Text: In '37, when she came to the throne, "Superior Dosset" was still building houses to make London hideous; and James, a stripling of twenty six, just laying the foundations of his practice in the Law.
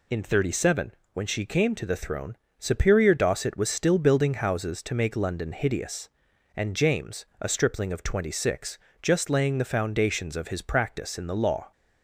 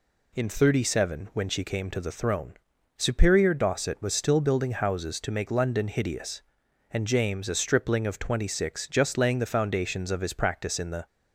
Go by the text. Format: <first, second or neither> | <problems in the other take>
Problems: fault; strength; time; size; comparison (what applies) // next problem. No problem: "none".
first | stops before "Law"; at 11.0 s